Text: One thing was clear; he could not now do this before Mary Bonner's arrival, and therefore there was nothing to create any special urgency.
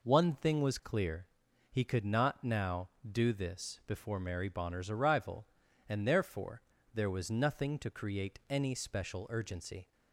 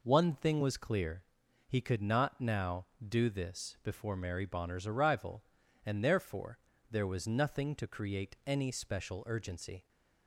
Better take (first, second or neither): neither